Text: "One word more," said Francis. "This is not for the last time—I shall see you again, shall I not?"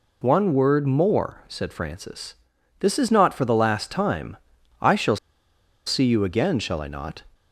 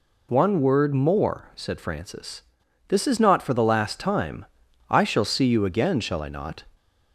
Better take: second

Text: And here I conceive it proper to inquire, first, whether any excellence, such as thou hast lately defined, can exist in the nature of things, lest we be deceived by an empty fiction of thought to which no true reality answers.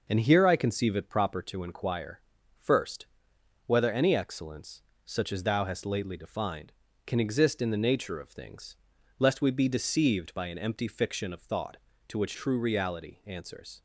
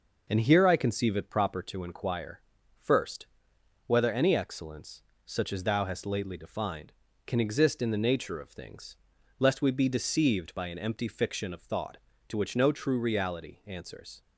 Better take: second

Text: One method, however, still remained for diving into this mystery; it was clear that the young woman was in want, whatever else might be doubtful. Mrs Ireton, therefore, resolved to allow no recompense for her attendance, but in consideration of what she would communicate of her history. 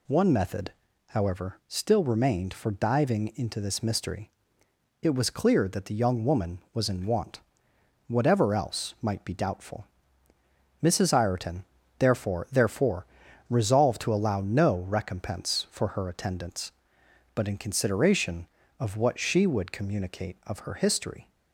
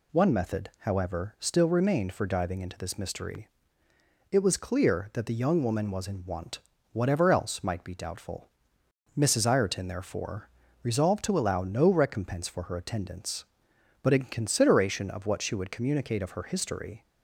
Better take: second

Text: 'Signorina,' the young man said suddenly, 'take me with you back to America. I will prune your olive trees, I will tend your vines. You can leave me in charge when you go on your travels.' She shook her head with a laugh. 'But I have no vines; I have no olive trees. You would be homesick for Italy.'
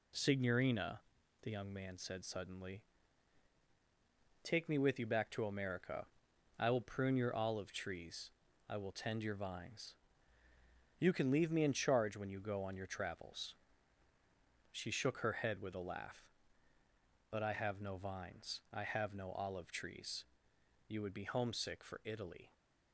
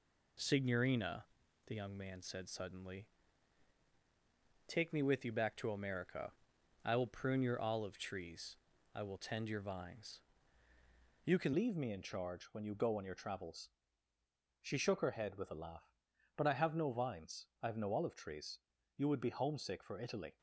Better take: first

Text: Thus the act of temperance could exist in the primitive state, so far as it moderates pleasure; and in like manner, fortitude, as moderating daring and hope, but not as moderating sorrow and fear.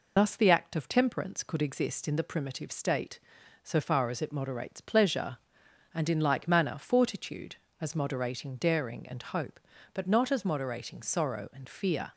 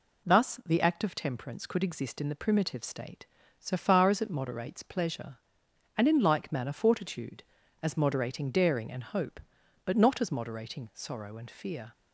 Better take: second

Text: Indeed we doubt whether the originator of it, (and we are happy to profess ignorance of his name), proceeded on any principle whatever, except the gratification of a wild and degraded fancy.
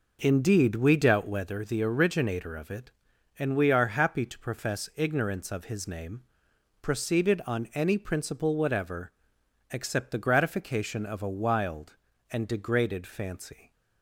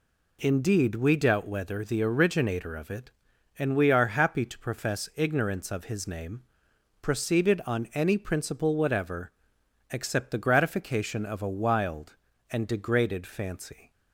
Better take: second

